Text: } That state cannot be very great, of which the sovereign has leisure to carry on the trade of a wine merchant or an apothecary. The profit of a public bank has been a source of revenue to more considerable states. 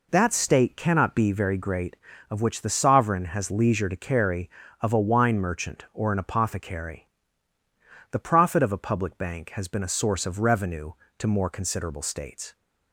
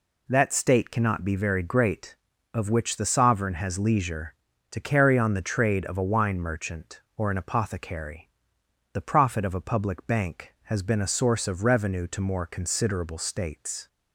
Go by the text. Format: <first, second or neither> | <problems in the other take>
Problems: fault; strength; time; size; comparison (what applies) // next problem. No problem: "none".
second | skips "on the trade"; at 4.6 s